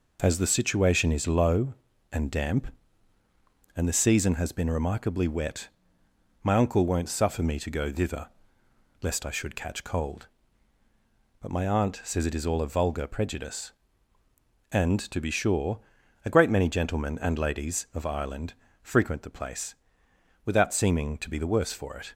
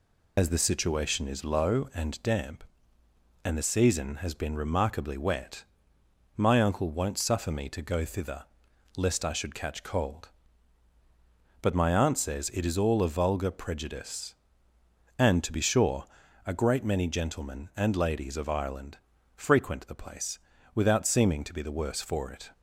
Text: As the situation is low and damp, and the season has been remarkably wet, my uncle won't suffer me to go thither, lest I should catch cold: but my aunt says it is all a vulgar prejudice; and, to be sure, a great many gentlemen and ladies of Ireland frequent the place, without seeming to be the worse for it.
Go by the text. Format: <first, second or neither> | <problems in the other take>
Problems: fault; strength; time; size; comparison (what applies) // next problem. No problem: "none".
first | loses the start of "As"; at 0.3 s; 70 ms // pauses between "Ireland" and "frequent"; slight; at 18.9 s; 0.36 s long; slight in the first